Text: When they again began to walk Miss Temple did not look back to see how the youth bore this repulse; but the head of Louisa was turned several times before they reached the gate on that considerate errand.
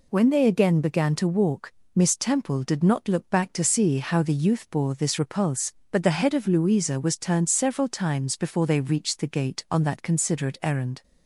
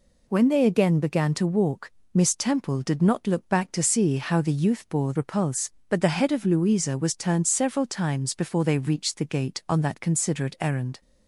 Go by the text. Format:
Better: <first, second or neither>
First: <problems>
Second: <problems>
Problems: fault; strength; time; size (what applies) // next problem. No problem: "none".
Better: first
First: pauses between "walk" and "Miss"; slight; at 1.7 s; 0.24 s long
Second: pauses between "walk" and "Miss"; slight; at 1.8 s; 0.24 s long // skips "this"; at 5.1 s